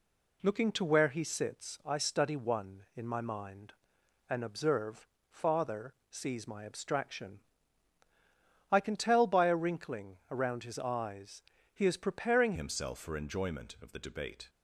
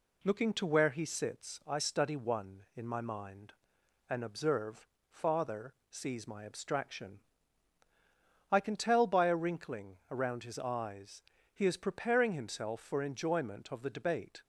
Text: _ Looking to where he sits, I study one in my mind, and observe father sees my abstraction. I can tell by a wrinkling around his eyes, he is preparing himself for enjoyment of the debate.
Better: second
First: pauses between "observe" and "father"; slight; at 5.0 s; 0.24 s long // pauses between "father" and "sees"; slight; at 5.9 s; 0.16 s long // pauses between "wrinkling" and "around"; slight; at 10.1 s; 0.16 s long // changes voice at "himself"; from 12.5 s on; 1.9 s long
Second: pauses between "observe" and "father"; slight; at 4.8 s; 0.24 s long // pauses between "father" and "sees"; slight; at 5.7 s; 0.16 s long // pauses between "wrinkling" and "around"; slight; at 9.9 s; 0.16 s long

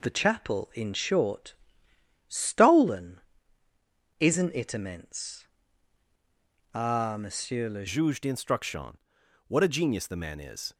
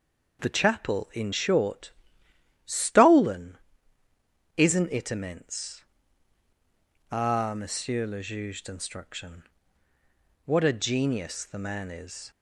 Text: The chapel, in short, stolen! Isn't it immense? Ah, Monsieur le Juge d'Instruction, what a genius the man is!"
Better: second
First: changes voice at "Juge"; from 7.8 s on; 2.9 s long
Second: none

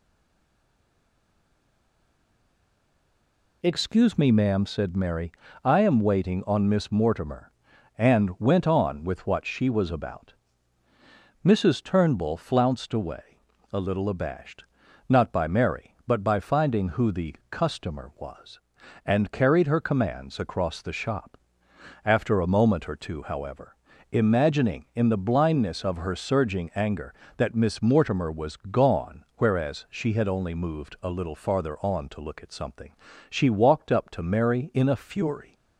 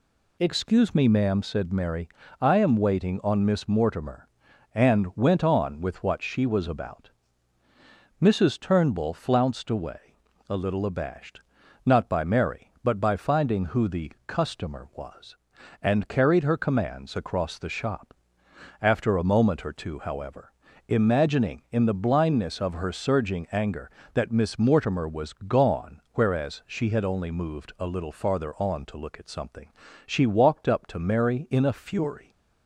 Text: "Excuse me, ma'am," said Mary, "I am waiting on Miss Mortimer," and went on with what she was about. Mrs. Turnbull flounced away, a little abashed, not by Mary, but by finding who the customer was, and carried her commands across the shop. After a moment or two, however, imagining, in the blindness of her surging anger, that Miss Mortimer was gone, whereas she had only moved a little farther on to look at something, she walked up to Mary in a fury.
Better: second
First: stays silent before the first word; strong; until 3.6 s; 3.6 s long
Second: none

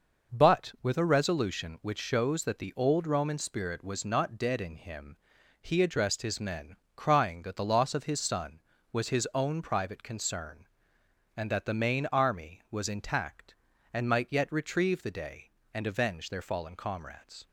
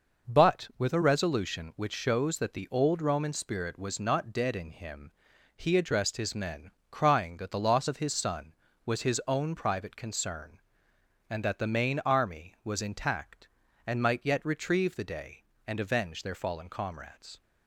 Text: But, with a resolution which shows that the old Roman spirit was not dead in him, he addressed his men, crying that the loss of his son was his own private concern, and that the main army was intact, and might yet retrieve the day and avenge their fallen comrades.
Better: neither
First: none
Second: none

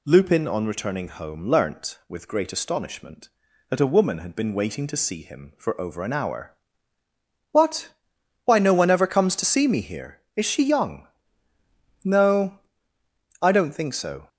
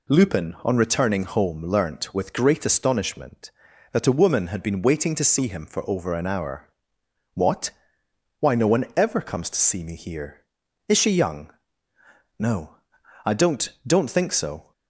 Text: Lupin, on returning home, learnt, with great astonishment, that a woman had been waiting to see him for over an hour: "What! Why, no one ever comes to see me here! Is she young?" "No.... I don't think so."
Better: first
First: none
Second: says "don't" twice; at 13.8 s

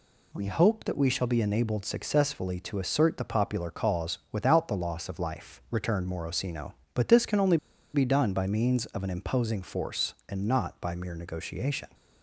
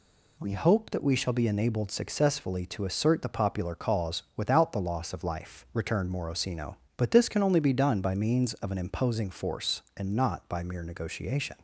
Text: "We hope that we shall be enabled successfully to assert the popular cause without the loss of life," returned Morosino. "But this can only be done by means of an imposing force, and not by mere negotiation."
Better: second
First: pauses between "only" and "be"; slight; at 7.5 s; 0.36 s long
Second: none

